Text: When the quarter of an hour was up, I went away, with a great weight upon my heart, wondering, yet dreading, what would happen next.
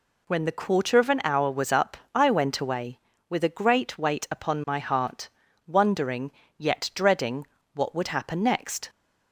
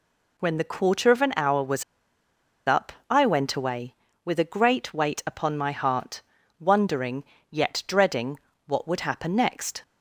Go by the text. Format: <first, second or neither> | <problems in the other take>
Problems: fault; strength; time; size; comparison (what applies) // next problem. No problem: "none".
first | pauses between "was" and "up"; noticeable; at 1.8 s; 0.83 s long